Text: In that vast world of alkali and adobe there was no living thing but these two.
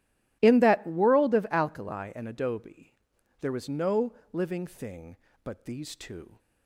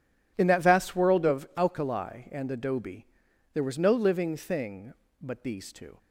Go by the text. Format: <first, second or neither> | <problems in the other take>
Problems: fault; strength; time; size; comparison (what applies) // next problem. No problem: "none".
second | starts louder than the rest; strong; until 1.4 s; 14 dB // skips "vast"; at 0.8 s // pauses between "adobe" and "there"; noticeable; at 2.9 s; 0.46 s long; noticeable in the second // pauses between "no" and "living"; slight; at 4.1 s; 0.20 s long